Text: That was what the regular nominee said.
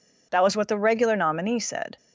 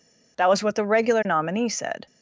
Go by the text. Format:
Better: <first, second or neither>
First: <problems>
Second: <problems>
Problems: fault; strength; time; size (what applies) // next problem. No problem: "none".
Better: neither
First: none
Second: none